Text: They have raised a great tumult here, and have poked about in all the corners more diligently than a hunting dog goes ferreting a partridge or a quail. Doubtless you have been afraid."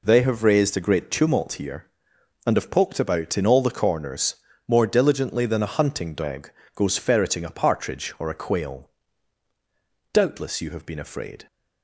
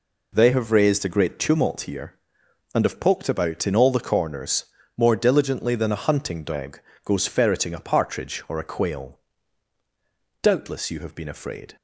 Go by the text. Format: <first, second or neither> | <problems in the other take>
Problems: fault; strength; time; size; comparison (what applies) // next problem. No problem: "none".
neither | pauses between "corners" and "more"; slight; the same in both // pauses between "dog" and "goes"; slight; the same in both